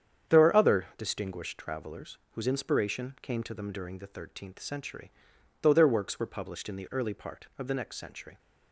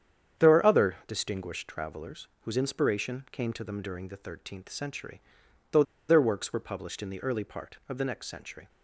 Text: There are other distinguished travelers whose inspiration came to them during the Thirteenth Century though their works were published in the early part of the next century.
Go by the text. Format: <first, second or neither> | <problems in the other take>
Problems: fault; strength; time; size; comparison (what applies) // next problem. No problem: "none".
first | starts louder than the rest; strong; until 1.4 s; 8.5 dB; strong in the first // pauses between "travelers" and "whose"; slight; at 2.2 s; 0.16 s long; slight in the first // pauses between "Century" and "though"; noticeable; at 5.1 s; 0.52 s long; noticeable in the first // pauses between "though" and "their"; slight; at 5.8 s; 0.26 s long